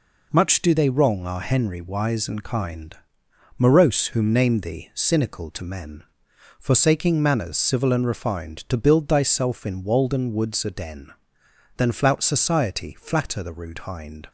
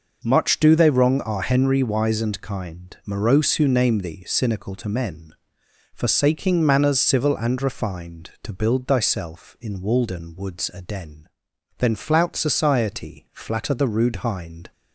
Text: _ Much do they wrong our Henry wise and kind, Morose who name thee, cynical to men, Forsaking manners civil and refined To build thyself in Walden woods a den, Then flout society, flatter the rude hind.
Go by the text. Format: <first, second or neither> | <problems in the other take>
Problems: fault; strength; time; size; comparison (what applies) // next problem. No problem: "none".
second | says "whom" for "who"; at 4.0 s